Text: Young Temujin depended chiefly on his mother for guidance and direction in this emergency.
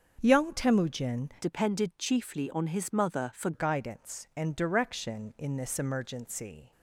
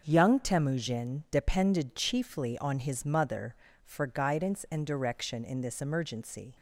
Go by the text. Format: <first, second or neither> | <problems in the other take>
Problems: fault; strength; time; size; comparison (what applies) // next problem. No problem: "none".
second | starts louder than the rest; until 1.2 s; 6.5 dB; noticeable in the second // changes voice from "depended" to "for"; from 1.4 to 3.5 s; 2.1 s long